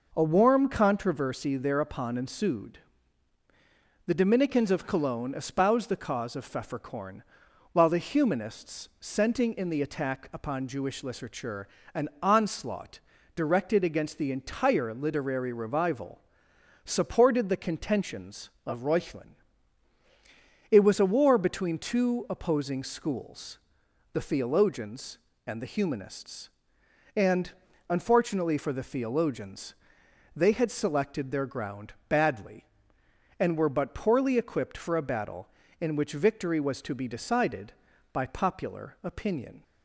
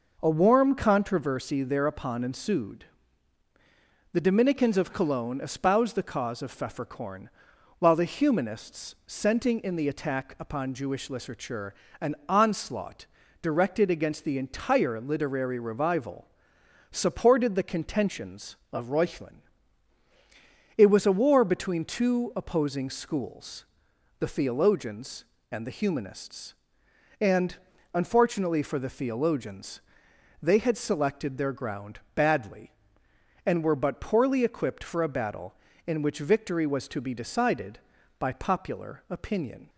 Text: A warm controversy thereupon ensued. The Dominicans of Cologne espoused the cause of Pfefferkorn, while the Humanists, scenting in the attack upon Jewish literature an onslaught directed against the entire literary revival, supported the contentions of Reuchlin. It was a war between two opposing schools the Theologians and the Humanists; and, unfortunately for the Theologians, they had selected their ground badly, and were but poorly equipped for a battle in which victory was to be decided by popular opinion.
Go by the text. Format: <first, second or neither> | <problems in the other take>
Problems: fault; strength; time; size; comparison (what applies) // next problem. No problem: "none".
neither | pauses between "literature" and "an"; slight; the same in both // pauses between "onslaught" and "directed"; the same in both // pauses between "schools" and "the"; noticeable; the same in both // pauses between "ground" and "badly"; slight; the same in both